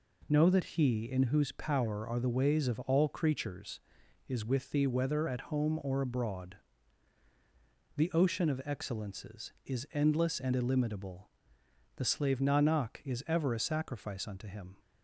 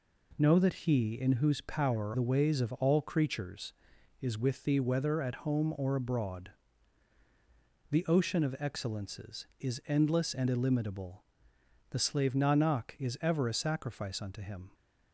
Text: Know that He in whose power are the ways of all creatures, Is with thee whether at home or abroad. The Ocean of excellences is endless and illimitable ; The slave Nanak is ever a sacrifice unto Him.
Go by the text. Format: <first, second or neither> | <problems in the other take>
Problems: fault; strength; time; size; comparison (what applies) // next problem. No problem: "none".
first | skips "are"; at 2.1 s